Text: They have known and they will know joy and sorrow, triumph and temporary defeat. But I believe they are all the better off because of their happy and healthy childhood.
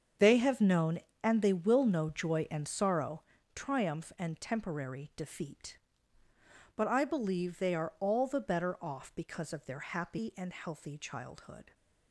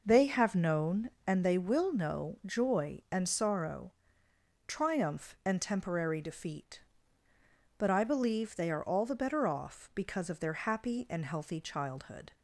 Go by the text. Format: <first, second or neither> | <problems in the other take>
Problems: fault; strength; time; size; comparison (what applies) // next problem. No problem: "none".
second | gets quieter; strong; throughout; 13 dB